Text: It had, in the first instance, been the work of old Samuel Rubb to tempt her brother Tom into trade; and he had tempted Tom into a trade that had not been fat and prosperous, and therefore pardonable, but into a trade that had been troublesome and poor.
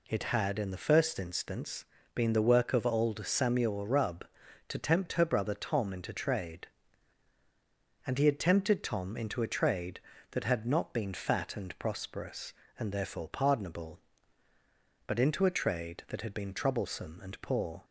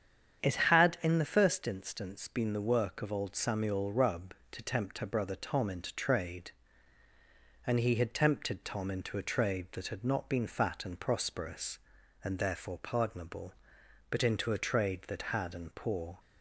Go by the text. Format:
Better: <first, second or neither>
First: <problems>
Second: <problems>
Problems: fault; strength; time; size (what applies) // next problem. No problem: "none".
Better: first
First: none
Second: starts louder than the rest; strong; until 1.4 s; 8.5 dB // skips "been troublesome"; at 15.5 s